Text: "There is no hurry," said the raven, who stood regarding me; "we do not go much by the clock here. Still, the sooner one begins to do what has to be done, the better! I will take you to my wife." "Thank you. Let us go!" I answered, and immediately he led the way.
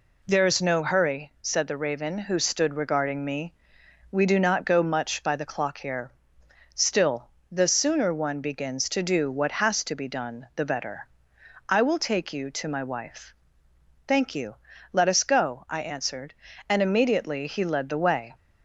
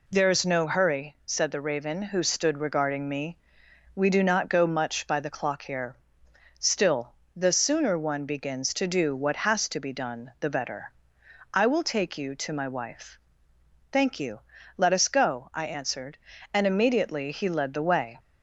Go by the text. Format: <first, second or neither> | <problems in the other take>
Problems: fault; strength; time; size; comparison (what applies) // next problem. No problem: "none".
neither | none